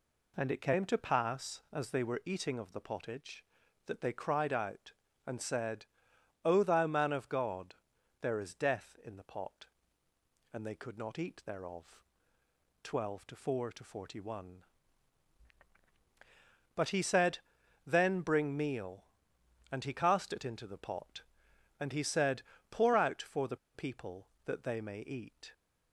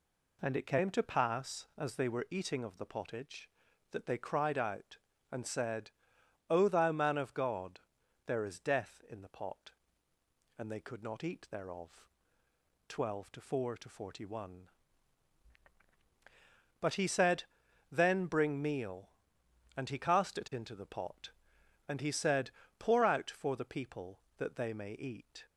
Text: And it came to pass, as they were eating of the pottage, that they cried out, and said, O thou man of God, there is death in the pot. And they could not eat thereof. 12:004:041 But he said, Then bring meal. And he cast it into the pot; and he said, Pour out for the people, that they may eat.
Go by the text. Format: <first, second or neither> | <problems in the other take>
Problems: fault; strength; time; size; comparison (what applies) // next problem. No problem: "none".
second | pauses between "the" and "people"; slight; at 23.5 s; 0.17 s long